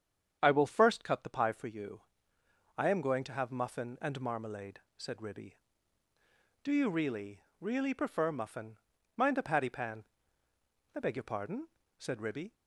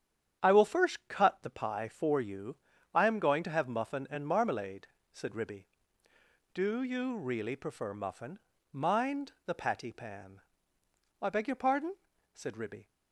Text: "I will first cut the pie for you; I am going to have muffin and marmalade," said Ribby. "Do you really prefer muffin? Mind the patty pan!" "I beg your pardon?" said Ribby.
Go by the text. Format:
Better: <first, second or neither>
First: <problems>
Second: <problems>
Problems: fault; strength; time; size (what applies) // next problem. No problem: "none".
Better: second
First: starts louder than the rest; strong; until 1.4 s; 8 dB // says "really" twice; at 7.5 s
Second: starts louder than the rest; strong; until 1.4 s; 9 dB